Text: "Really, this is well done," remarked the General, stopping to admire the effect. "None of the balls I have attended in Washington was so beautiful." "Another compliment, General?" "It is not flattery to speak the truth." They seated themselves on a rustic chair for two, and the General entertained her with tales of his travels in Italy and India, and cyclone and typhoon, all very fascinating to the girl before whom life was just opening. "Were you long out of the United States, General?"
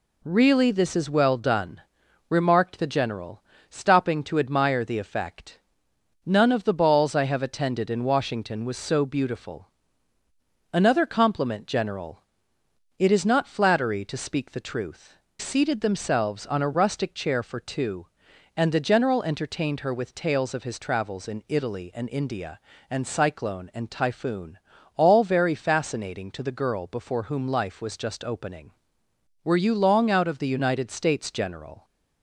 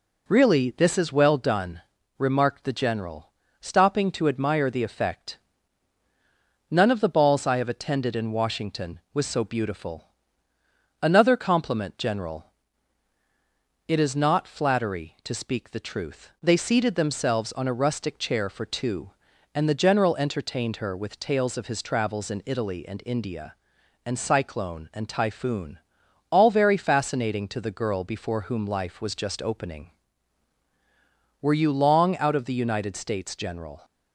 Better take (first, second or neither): second